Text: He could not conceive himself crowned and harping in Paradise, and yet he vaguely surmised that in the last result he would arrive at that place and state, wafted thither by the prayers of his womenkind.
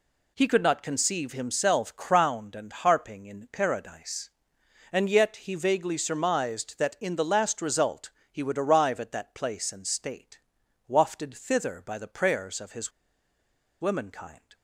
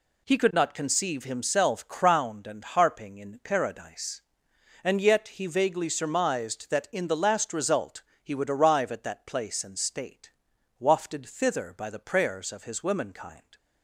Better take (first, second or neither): second